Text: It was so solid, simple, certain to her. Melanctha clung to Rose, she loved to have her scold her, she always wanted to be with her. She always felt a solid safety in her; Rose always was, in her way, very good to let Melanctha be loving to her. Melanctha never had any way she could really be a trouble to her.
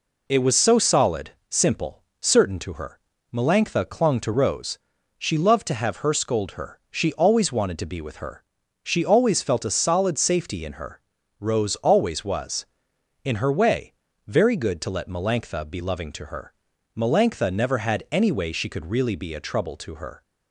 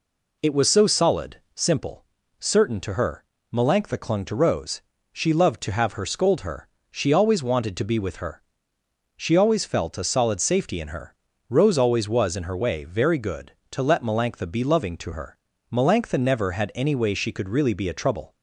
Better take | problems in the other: first | stops before "to her"; at 18.3 s

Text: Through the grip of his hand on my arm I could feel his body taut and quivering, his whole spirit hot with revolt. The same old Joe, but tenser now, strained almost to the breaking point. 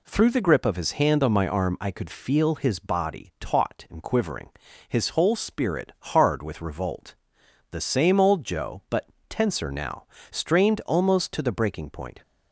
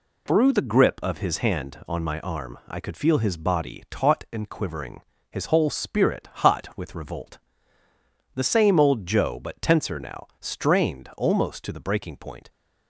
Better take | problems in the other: second | says "hard" for "hot"; at 5.9 s // pauses between "but" and "tenser"; slight; at 9.0 s; 0.24 s long

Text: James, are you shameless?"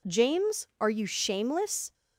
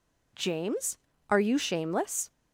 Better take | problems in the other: neither | none

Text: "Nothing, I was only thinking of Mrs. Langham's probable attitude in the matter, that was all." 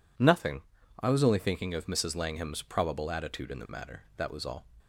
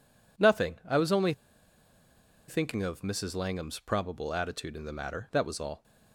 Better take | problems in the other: first | pauses between "only" and "thinking"; at 1.3 s; 1.1 s long

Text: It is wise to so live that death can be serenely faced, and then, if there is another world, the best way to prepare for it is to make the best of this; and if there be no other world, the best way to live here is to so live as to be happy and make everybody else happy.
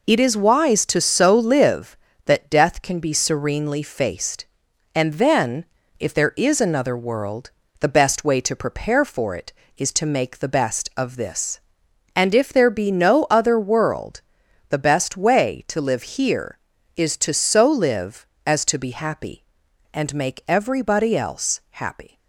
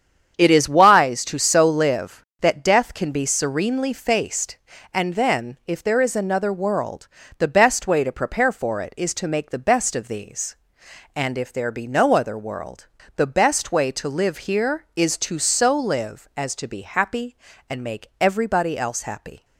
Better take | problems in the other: first | starts louder than the rest; strong; until 1.3 s; 8 dB // says "these" for "this"; at 10.0 s

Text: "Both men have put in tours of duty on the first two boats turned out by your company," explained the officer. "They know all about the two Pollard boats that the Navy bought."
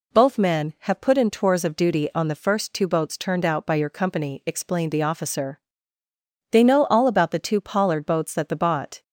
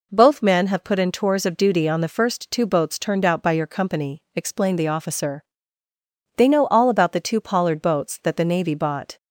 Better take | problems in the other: second | skips "Navy"; at 8.5 s

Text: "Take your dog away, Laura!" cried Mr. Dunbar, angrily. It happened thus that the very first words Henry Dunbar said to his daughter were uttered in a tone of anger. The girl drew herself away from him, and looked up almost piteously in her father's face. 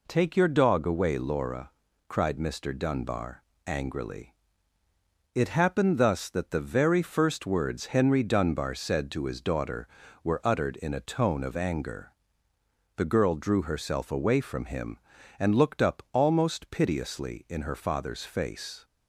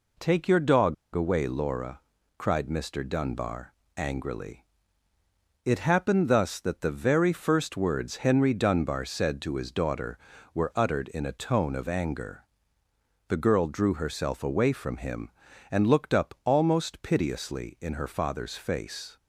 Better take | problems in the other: first | pauses between "dog" and "away"; slight; at 0.9 s; 0.19 s long

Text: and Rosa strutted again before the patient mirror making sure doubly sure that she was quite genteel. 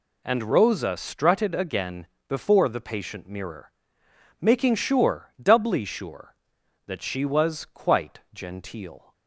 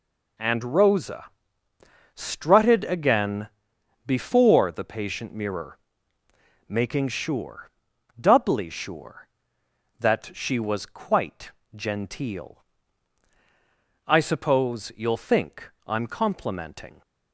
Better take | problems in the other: first | pauses between "Rosa" and "strutted"; noticeable; at 1.2 s; 0.90 s long // pauses between "again" and "before"; noticeable; at 3.4 s; 0.56 s long; slight in the first // pauses between "mirror" and "making"; noticeable; at 5.7 s; 0.90 s long; noticeable in the first // pauses between "sure" and "doubly"; noticeable; at 7.6 s; 0.50 s long // pauses between "quite" and "genteel"; slight; at 11.5 s; 0.22 s long // goes on to say "I suppose you'll think I'm complimenting"; strong; from 14.0 s on; 2.9 s long

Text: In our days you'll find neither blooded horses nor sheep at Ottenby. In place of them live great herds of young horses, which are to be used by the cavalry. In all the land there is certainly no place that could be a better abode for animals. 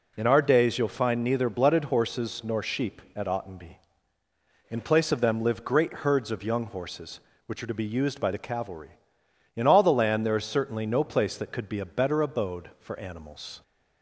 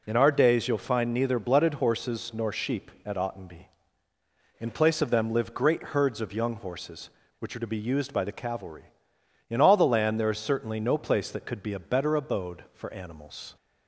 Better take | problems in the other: neither | none

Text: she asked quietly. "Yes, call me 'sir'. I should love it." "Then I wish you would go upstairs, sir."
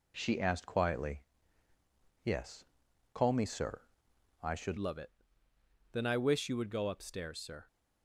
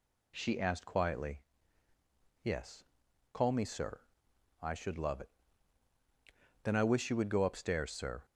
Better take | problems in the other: second | changes voice at "love"; from 4.7 s on; 2.9 s long

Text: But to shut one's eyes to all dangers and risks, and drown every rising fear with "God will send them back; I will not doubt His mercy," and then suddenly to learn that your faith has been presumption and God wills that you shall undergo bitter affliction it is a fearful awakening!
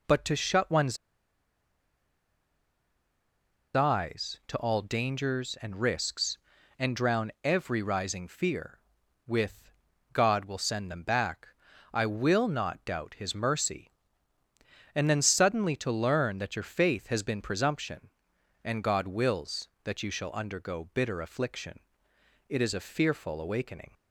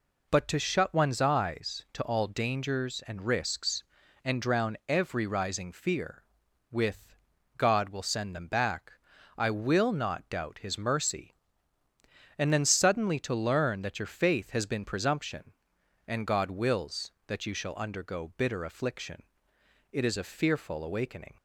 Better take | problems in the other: second | pauses between "one's" and "eyes"; strong; at 0.9 s; 2.7 s long // pauses between "with" and "God"; at 9.7 s; 0.44 s long; also in the second // pauses between "affliction" and "it"; noticeable; at 21.8 s; 0.68 s long; noticeable in the second

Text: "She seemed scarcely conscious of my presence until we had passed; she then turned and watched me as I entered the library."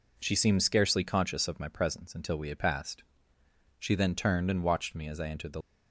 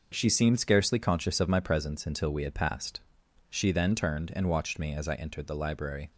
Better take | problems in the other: second | stops before "library"; at 5.6 s

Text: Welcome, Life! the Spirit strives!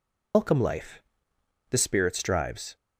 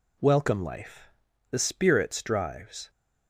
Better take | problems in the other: second | loses the start of "Welcome"; at 0.3 s; 135 ms

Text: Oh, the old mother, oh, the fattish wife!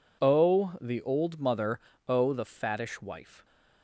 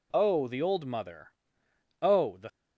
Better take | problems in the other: first | stops before "fattish wife"; at 2.4 s

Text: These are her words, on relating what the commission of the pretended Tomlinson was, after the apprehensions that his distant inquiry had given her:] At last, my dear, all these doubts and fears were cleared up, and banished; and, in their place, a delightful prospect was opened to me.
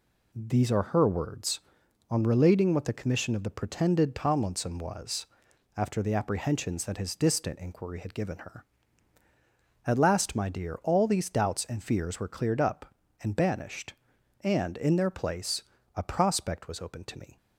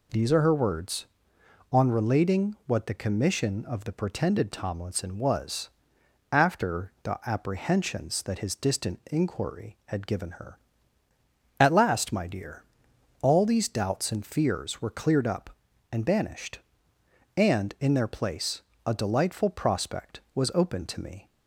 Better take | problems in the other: second | skips "delightful"; at 16.0 s

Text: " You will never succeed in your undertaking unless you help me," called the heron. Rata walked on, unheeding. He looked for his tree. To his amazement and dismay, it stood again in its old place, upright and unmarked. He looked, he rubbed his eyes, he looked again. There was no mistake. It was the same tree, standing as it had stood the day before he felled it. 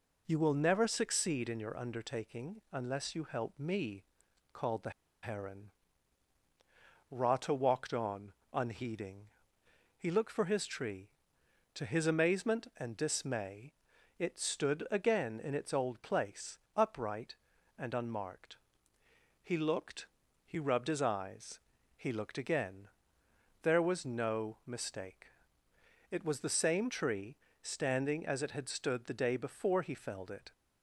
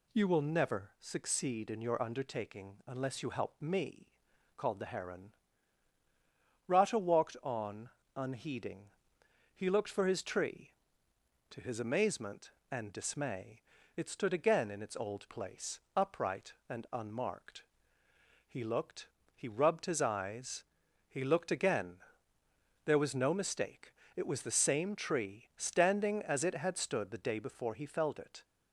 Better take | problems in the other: second | pauses between "the" and "heron"; slight; at 4.8 s; 0.32 s long

